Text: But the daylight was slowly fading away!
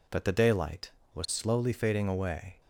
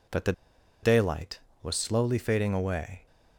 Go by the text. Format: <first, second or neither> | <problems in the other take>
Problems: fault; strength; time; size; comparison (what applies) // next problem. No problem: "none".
first | pauses between "the" and "daylight"; noticeable; at 0.3 s; 0.50 s long